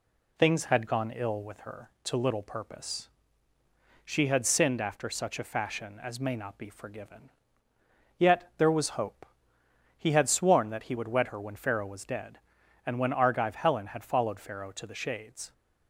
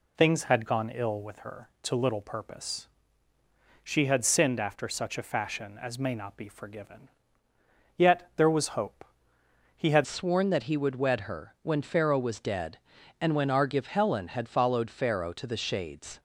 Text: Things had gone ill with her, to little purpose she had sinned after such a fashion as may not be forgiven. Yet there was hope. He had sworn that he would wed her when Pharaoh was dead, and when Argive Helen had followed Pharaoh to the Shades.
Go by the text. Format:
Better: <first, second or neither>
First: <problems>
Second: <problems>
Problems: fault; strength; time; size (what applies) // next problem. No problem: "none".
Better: first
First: pauses between "purpose" and "she"; at 3.0 s; 1.0 s long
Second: pauses between "purpose" and "she"; at 2.8 s; 1.0 s long // changes voice at "sworn"; from 10.0 s on; 6.1 s long